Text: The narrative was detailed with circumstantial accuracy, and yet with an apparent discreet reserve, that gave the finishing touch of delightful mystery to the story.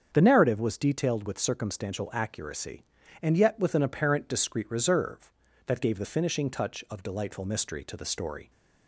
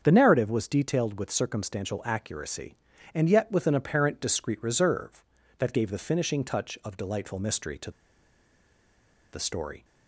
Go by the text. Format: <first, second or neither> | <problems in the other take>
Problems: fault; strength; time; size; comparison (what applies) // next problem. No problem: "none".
first | starts louder than the rest; strong; until 1.0 s; 7.5 dB; strong in the first // pauses between "to" and "the"; strong; at 7.8 s; 1.4 s long